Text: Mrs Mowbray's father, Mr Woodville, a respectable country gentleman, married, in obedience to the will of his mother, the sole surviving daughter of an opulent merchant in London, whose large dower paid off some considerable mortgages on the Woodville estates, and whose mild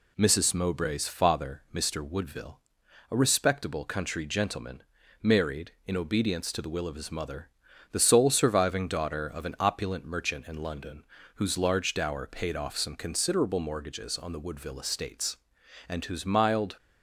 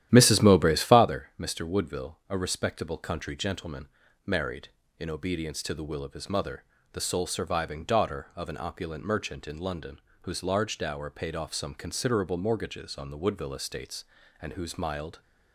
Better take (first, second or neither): first